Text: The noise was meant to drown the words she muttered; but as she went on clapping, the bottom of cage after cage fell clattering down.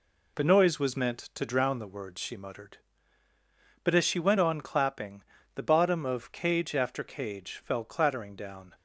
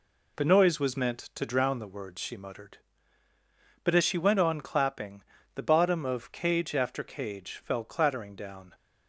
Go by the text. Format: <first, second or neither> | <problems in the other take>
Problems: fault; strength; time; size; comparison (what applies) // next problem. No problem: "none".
neither | none